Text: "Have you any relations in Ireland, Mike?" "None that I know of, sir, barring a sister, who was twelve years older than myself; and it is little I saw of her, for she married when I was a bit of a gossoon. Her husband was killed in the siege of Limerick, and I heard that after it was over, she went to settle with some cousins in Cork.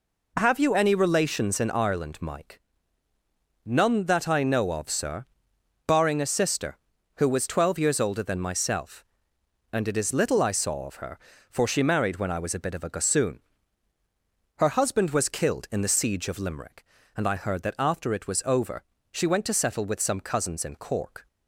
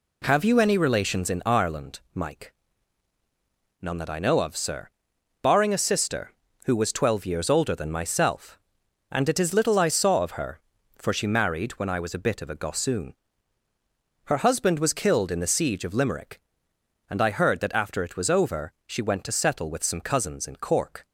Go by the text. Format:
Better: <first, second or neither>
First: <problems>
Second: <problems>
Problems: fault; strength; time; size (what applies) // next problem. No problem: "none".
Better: neither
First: none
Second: none